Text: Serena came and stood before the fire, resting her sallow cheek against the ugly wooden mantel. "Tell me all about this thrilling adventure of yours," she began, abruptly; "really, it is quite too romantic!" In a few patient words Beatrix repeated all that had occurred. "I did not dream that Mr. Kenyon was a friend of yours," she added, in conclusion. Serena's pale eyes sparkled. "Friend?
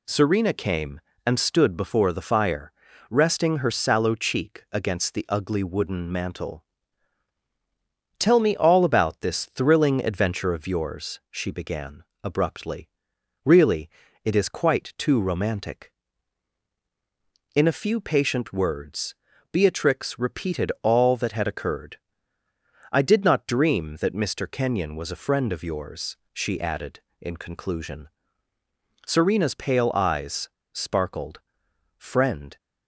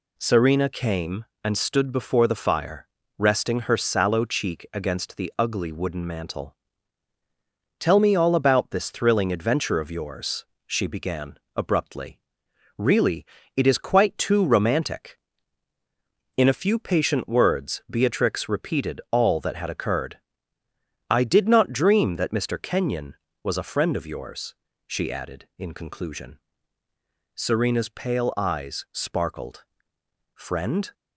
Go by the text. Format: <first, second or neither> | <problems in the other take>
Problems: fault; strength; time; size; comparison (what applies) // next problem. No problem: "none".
second | pauses between "words" and "Beatrix"; at 19.1 s; 0.38 s long // pauses between "eyes" and "sparkled"; slight; at 30.4 s; 0.24 s long